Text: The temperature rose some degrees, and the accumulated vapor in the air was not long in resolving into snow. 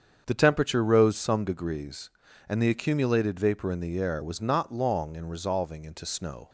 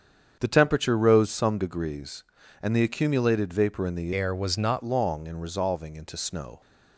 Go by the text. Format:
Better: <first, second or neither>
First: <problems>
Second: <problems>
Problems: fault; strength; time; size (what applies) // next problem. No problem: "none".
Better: first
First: starts louder than the rest; strong; until 1.2 s; 7.5 dB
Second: starts louder than the rest; strong; until 1.4 s; 7.5 dB // changes voice from "air" to "not"; from 4.1 to 4.8 s; 0.7 s long